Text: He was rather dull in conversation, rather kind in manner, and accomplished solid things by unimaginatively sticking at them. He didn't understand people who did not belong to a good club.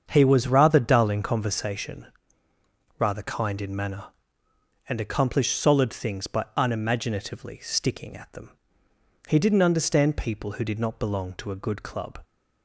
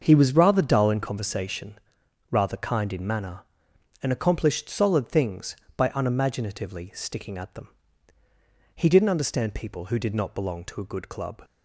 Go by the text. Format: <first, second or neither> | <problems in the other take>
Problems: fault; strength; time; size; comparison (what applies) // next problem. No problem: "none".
neither | starts louder than the rest; the same in both